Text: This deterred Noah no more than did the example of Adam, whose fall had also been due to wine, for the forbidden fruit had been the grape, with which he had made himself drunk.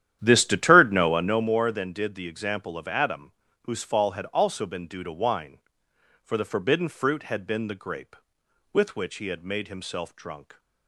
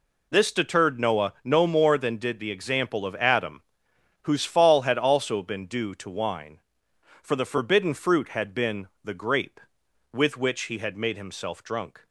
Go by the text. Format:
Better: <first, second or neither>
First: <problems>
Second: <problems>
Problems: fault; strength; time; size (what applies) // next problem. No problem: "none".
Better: second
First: starts louder than the rest; strong; until 1.5 s; 11 dB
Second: none